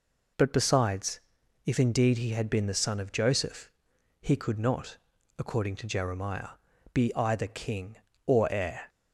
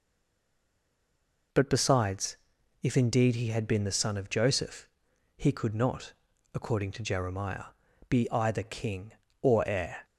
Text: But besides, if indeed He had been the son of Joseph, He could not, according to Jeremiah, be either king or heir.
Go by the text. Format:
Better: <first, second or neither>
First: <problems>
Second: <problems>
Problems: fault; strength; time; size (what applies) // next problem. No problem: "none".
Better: first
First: none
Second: stays silent before the first word; noticeable; until 1.5 s; 1.5 s long